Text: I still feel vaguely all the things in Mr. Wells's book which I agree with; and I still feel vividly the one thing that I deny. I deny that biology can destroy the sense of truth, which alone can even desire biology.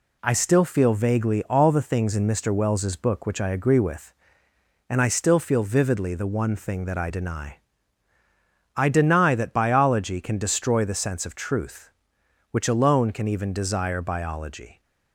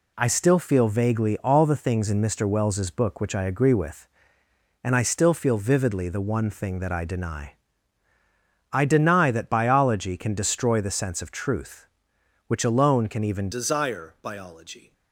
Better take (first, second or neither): first